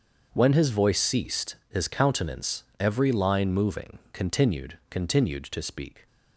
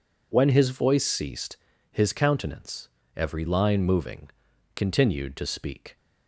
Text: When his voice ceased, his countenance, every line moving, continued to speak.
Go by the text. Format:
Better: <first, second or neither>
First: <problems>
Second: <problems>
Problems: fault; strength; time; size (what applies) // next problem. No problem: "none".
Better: second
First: starts louder than the rest; until 1.3 s; 6.5 dB // says "continued" twice; at 4.8 s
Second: none